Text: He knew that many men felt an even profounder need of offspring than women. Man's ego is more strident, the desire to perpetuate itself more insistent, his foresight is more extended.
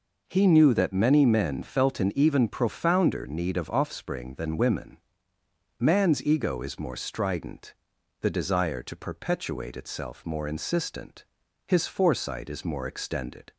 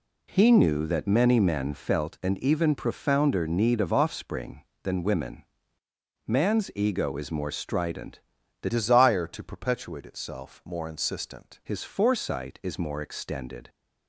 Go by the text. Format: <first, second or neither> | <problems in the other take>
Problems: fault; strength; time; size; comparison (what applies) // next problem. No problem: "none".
first | changes voice from "desire" to "insistent"; from 8.6 to 11.5 s; 2.9 s long